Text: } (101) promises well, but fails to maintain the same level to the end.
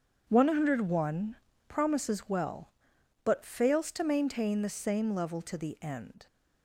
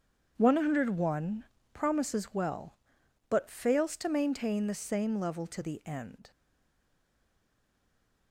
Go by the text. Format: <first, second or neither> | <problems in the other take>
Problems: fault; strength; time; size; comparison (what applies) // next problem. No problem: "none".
first | starts louder than the rest; strong; until 1.3 s; 7.5 dB; strong in the first // stays silent after the last word; noticeable; from 6.3 s on; 2.0 s long